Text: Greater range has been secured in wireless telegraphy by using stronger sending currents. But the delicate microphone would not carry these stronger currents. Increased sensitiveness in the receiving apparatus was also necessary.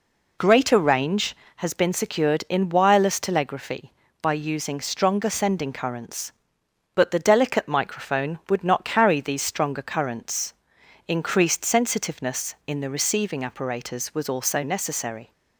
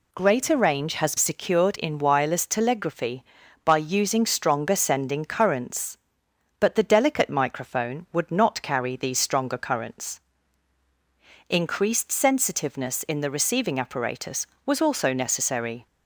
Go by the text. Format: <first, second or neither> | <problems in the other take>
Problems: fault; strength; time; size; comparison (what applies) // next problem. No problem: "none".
first | skips "been"; at 1.1 s